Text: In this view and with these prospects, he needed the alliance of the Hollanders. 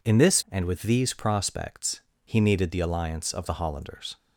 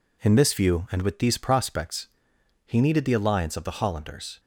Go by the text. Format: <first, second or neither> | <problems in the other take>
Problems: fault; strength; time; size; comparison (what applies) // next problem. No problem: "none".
second | skips "view"; at 0.4 s